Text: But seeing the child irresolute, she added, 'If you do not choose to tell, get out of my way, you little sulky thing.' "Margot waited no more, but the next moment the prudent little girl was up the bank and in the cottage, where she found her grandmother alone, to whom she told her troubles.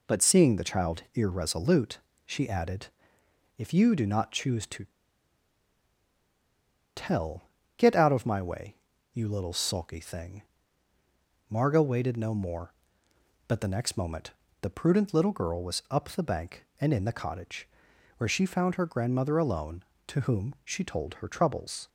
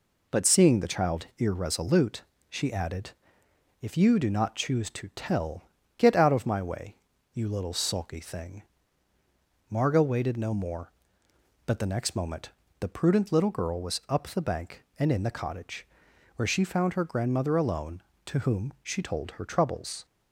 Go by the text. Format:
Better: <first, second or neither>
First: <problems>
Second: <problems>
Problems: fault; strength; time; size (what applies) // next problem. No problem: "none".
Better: second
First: pauses between "to" and "tell"; strong; at 4.8 s; 2.1 s long // pauses between "moment" and "the"; slight; at 14.3 s; 0.30 s long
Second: pauses between "moment" and "the"; slight; at 12.5 s; 0.30 s long